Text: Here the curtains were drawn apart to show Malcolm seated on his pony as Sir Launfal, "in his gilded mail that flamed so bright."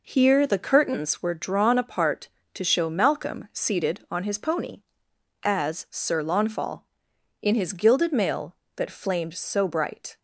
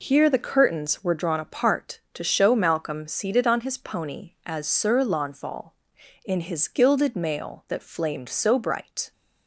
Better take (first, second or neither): neither